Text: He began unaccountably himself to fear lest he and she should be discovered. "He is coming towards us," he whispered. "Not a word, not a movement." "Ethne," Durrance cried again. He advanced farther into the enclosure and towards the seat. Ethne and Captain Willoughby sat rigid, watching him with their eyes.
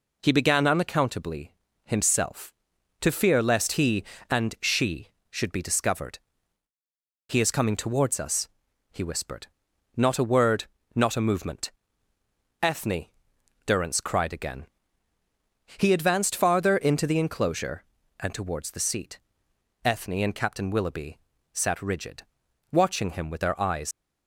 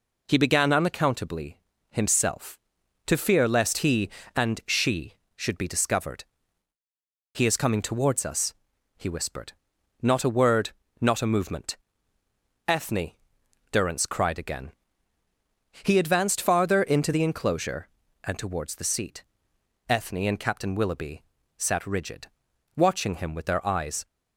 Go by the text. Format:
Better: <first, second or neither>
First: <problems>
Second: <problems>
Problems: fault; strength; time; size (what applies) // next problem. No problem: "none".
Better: second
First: pauses between "unaccountably" and "himself"; slight; at 1.5 s; 0.34 s long // pauses between "Willoughby" and "sat"; slight; at 21.1 s; 0.36 s long // leaves "eyes" unfinished; at 23.9 s; 90 ms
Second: pauses between "unaccountably" and "himself"; slight; at 1.5 s; 0.34 s long // pauses between "Willoughby" and "sat"; slight; at 21.2 s; 0.36 s long